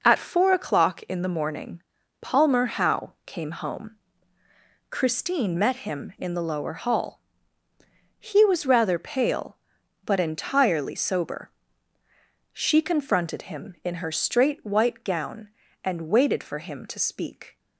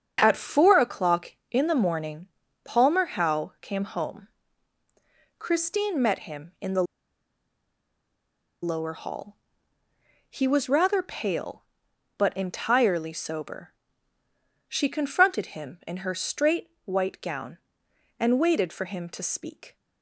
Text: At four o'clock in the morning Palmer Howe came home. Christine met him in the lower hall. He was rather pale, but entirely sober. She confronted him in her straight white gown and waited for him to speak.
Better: first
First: pauses between "morning" and "Palmer"; at 1.8 s; 0.40 s long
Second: starts louder than the rest; strong; until 1.2 s; 7 dB // pauses between "morning" and "Palmer"; at 2.2 s; 0.38 s long // pauses between "the" and "lower"; strong; at 6.8 s; 1.7 s long // pauses between "straight" and "white"; slight; at 16.6 s; 0.16 s long

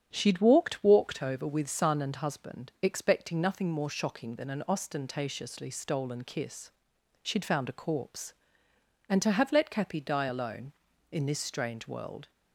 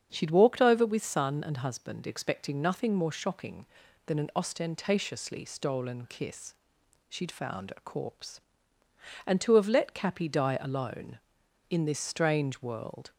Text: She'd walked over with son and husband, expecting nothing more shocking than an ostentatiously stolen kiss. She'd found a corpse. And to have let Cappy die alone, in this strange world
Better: second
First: starts louder than the rest; strong; until 1.1 s; 8 dB // says "walked" twice; at 0.8 s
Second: starts louder than the rest; strong; until 1.1 s; 7.5 dB

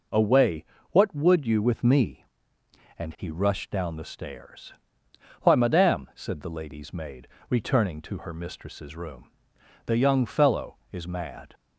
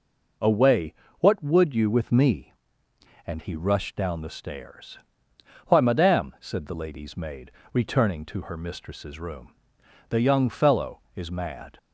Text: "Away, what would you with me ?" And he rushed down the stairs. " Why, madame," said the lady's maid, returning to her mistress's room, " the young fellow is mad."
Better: neither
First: starts louder than the rest; until 1.4 s; 6.5 dB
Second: starts louder than the rest; until 1.6 s; 6.5 dB

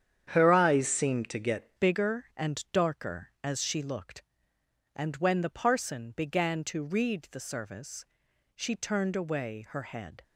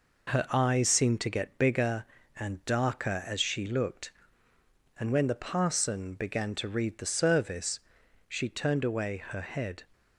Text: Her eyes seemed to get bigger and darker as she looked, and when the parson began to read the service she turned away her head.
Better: second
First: starts louder than the rest; strong; until 1.3 s; 8.5 dB // changes voice at "bigger"; from 1.7 s on; 8.5 s long // pauses between "service" and "she"; noticeable; at 8.0 s; 0.50 s long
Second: pauses between "service" and "she"; noticeable; at 7.7 s; 0.48 s long

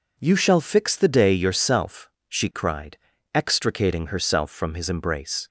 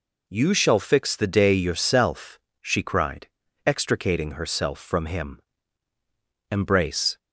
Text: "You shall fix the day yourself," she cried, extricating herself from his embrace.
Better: first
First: none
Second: says "him" for "his"; at 5.0 s

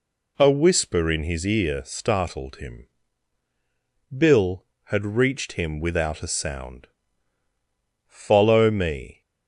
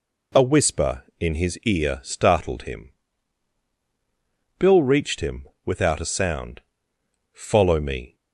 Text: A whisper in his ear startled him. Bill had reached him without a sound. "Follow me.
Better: first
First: none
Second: skips "had"; at 4.8 s // pauses between "him" and "without"; slight; at 5.4 s; 0.18 s long

